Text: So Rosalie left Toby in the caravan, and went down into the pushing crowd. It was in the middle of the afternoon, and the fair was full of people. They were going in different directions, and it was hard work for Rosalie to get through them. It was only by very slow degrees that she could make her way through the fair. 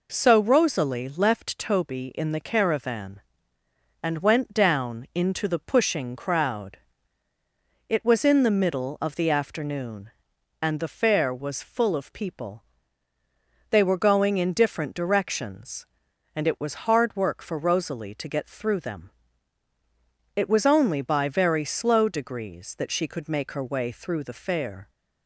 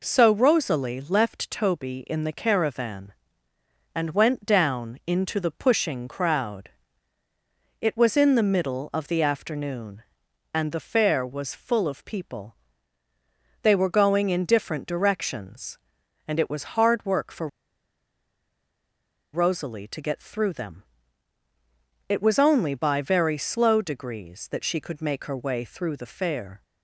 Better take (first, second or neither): first